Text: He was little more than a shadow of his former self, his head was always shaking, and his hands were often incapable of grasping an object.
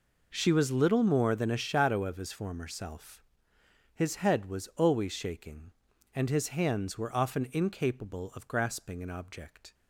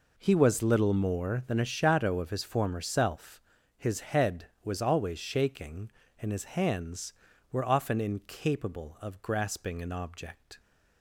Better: second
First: says "She" for "He"; at 0.3 s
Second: none

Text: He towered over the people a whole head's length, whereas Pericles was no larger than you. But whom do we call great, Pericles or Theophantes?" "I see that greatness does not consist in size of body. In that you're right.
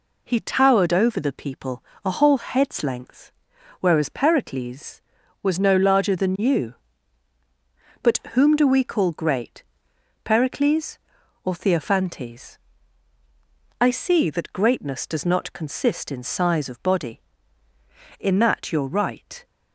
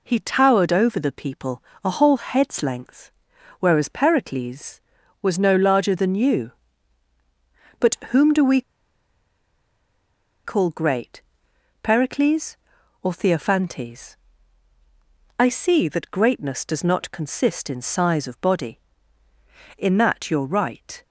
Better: first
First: pauses between "people" and "a"; slight; at 1.8 s; 0.20 s long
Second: pauses between "people" and "a"; slight; at 1.6 s; 0.20 s long // pauses between "we" and "call"; strong; at 8.6 s; 1.8 s long

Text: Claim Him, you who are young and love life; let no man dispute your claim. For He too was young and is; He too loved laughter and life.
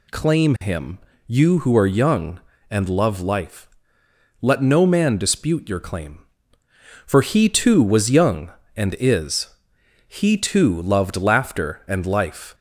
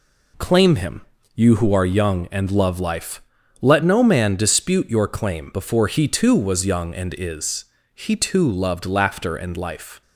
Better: first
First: none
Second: says "Before" for "For"; at 5.5 s

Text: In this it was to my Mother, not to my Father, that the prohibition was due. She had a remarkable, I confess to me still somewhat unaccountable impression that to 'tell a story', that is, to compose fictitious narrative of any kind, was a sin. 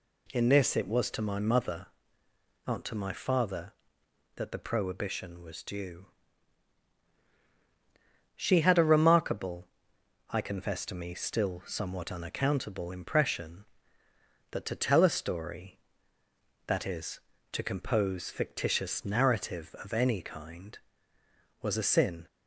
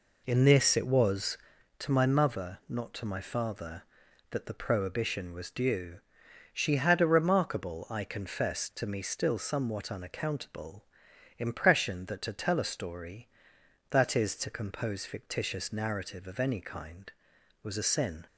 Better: first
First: none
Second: starts louder than the rest; until 1.7 s; 4 dB // pauses between "unaccountable" and "impression"; noticeable; at 10.8 s; 0.52 s long

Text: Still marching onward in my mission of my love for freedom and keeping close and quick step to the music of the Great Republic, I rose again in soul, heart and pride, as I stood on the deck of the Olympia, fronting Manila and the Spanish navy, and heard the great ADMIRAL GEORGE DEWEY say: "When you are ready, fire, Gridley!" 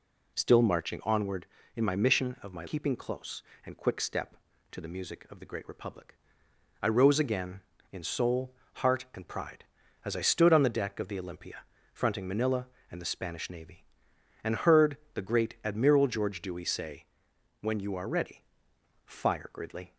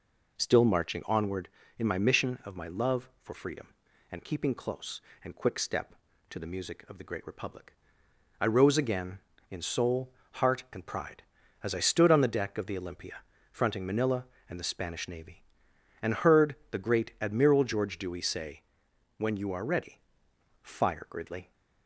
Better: second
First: skips "love for freedom and"; at 2.6 s // pauses between "heard" and "the"; slight; at 14.9 s; 0.20 s long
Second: pauses between "heard" and "the"; slight; at 16.5 s; 0.18 s long

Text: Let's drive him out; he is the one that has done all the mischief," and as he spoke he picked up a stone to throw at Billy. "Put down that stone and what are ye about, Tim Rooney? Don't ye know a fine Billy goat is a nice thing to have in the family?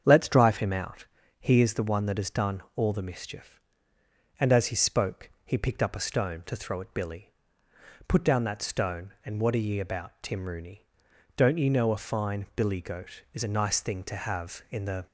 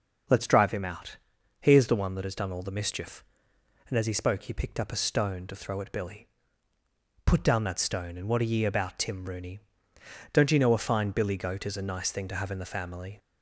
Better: second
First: starts louder than the rest; strong; until 1.0 s; 7.5 dB // pauses between "done" and "all"; slight; at 2.6 s; 0.16 s long // pauses between "spoke" and "he"; slight; at 5.3 s; 0.16 s long // stops before "family"; at 15.0 s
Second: starts louder than the rest; noticeable; until 1.7 s; 6 dB

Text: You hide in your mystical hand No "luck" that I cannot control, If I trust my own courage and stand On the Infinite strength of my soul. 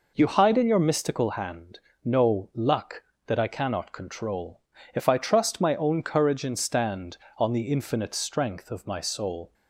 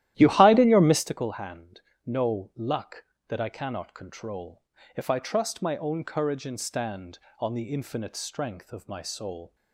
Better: first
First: pauses between "hand" and "No"; slight; at 1.7 s; 0.26 s long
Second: starts louder than the rest; strong; until 1.1 s; 13.5 dB // pauses between "hand" and "No"; slight; at 1.8 s; 0.26 s long

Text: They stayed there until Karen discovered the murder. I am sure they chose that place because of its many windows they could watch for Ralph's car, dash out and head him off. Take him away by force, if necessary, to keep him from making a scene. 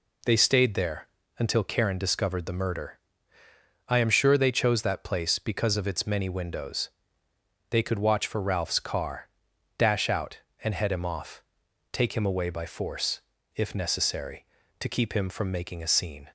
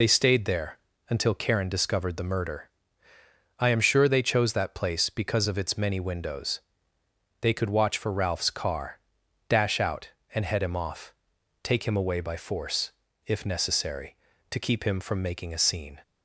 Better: first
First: pauses between "there" and "until"; slight; at 1.0 s; 0.32 s long // pauses between "windows" and "they"; noticeable; at 6.9 s; 0.80 s long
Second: loses the start of "They"; at 0.0 s; 60 ms // pauses between "there" and "until"; slight; at 0.7 s; 0.32 s long // pauses between "windows" and "they"; noticeable; at 6.6 s; 0.80 s long

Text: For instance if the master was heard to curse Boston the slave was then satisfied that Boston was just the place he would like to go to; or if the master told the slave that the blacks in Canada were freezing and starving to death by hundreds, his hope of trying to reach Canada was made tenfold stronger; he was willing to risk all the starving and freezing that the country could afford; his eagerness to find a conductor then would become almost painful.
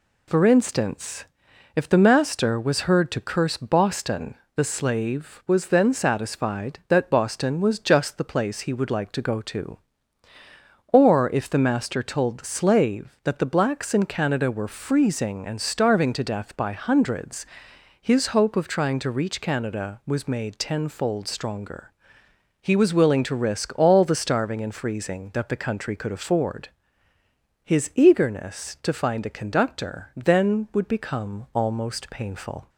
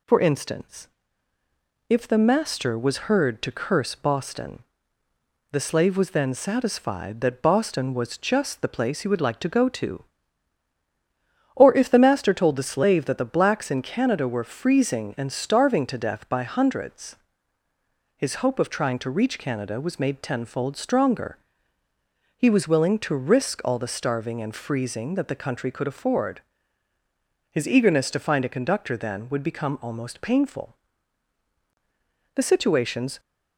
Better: first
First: pauses between "instance" and "if"; noticeable; at 1.2 s; 0.50 s long // pauses between "Boston" and "the"; slight; at 4.3 s; 0.22 s long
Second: pauses between "instance" and "if"; at 0.8 s; 1.0 s long // pauses between "Boston" and "the"; noticeable; at 4.5 s; 0.92 s long // goes on to say "The situations"; noticeable; from 32.3 s on; 0.86 s long

